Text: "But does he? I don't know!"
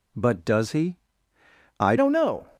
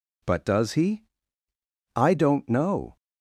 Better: second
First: changes voice at "don't"; from 1.9 s on; 0.5 s long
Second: none

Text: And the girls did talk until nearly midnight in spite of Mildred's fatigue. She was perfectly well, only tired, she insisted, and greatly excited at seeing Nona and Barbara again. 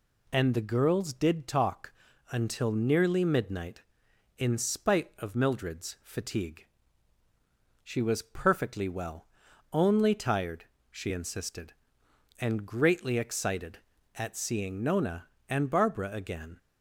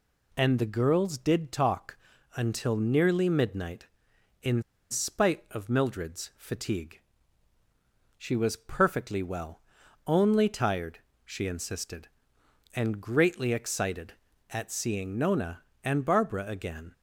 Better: first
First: pauses between "talk" and "until"; at 1.9 s; 0.38 s long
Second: pauses between "talk" and "until"; at 1.9 s; 0.38 s long // pauses between "in" and "spite"; slight; at 4.6 s; 0.27 s long

